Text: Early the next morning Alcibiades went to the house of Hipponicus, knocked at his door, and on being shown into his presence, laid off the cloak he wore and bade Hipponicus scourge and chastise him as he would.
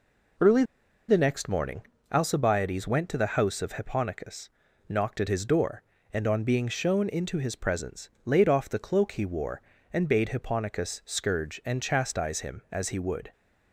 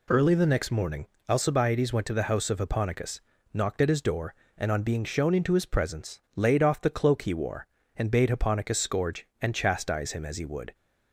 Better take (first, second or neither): second